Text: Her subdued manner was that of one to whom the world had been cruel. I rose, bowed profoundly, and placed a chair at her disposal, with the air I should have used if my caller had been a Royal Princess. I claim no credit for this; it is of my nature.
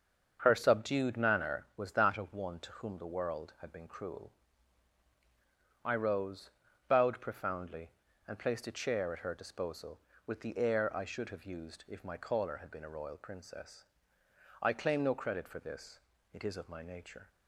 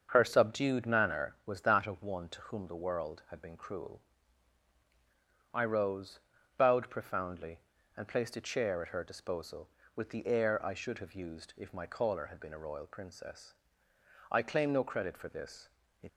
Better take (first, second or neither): first